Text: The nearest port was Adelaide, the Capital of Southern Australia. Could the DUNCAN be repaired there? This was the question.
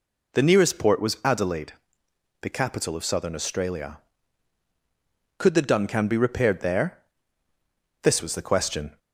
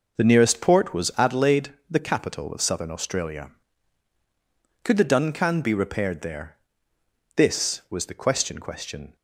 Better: first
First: none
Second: says "question" twice; at 8.5 s

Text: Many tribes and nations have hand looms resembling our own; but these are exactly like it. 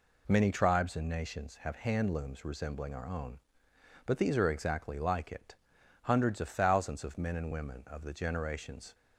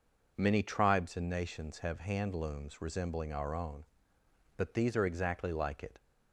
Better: second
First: goes on to say "Hundreds of thousands of men and women of the generations"; strong; from 6.0 s on; 2.8 s long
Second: none

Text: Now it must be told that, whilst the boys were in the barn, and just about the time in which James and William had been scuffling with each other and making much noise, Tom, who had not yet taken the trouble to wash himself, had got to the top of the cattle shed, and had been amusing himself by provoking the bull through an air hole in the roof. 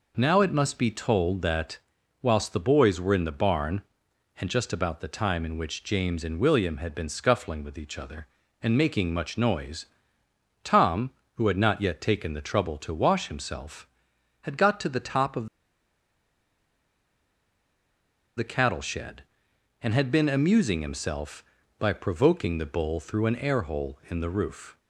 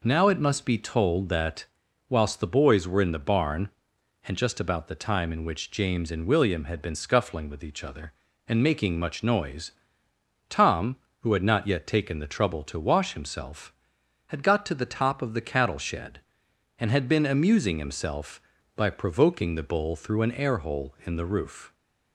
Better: second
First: pauses between "of" and "the"; strong; at 15.4 s; 2.8 s long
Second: none

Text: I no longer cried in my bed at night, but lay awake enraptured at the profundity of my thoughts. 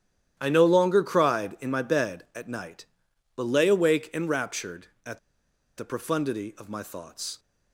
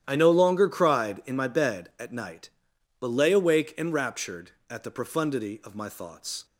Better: second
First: starts louder than the rest; strong; until 1.3 s; 11 dB // pauses between "at" and "the"; noticeable; at 5.1 s; 0.60 s long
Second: starts louder than the rest; strong; until 1.0 s; 11 dB

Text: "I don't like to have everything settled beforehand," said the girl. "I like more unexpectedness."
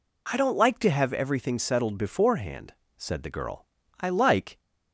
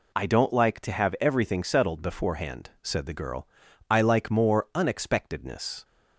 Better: second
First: stops before "more unexpectedness"; at 4.5 s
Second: none

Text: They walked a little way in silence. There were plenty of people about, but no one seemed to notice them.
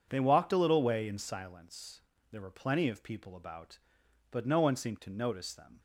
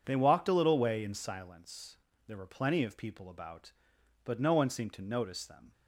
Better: neither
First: none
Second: none

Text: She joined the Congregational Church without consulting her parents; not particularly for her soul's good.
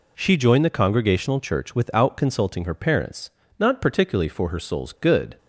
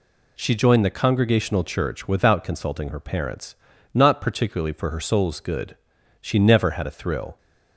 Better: first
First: none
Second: goes on to say "She never had a thrill"; noticeable; from 6.2 s on; 1.1 s long

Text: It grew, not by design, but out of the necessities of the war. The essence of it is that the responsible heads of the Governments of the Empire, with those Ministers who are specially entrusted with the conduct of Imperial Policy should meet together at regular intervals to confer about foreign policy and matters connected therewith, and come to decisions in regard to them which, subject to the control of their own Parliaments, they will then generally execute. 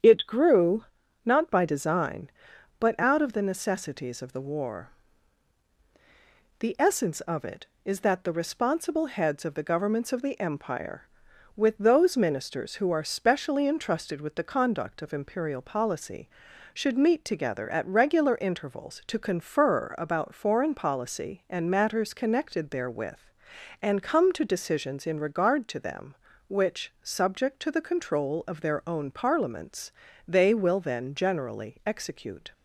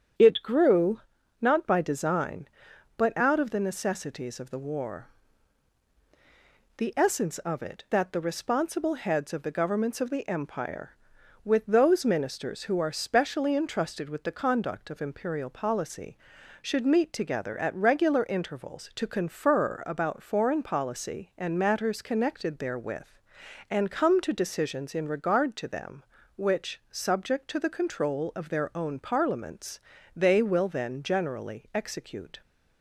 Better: first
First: starts louder than the rest; strong; until 1.4 s; 8.5 dB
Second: starts louder than the rest; strong; until 1.6 s; 8.5 dB // skips "is"; at 7.8 s

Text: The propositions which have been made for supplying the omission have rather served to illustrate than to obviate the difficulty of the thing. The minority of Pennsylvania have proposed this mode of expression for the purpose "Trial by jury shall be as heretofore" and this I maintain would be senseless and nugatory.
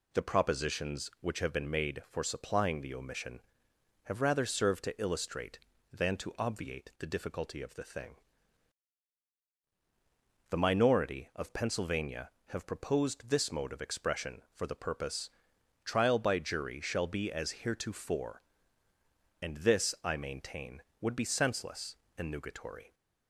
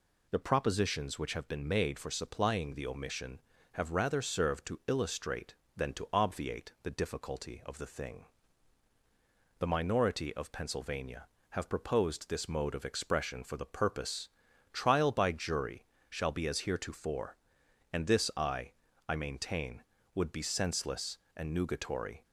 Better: first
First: pauses between "purpose" and "Trial"; noticeable; at 15.2 s; 0.54 s long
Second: pauses between "purpose" and "Trial"; at 14.2 s; 0.44 s long // pauses between "jury" and "shall"; slight; at 15.8 s; 0.24 s long // says "I" twice; at 19.0 s

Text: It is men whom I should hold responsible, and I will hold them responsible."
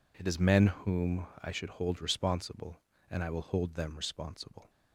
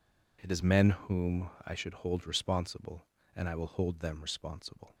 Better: neither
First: pauses between "whom" and "I"; slight; at 1.2 s; 0.16 s long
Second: pauses between "whom" and "I"; slight; at 1.4 s; 0.16 s long

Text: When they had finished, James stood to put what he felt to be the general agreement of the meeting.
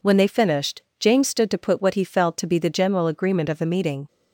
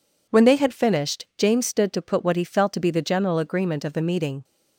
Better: second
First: skips "had"; at 0.2 s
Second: none

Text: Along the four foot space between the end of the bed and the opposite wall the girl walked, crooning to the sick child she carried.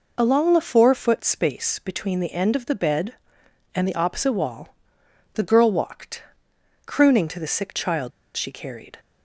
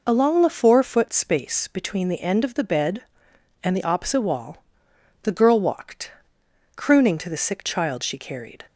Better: second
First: pauses between "wall" and "the"; noticeable; at 4.7 s; 0.60 s long // pauses between "child" and "she"; slight; at 8.1 s; 0.24 s long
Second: pauses between "wall" and "the"; noticeable; at 4.6 s; 0.60 s long

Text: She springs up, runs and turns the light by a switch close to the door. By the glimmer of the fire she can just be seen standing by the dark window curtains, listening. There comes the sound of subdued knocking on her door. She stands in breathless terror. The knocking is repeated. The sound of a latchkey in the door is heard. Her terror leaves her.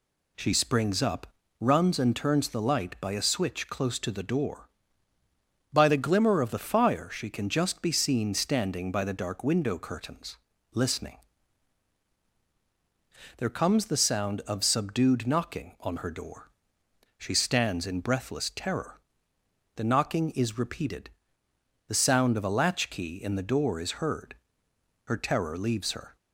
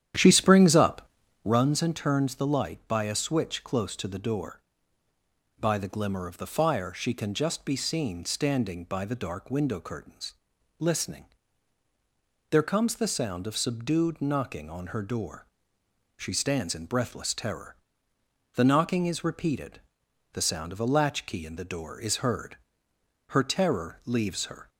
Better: first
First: none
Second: starts louder than the rest; strong; until 1.6 s; 10.5 dB

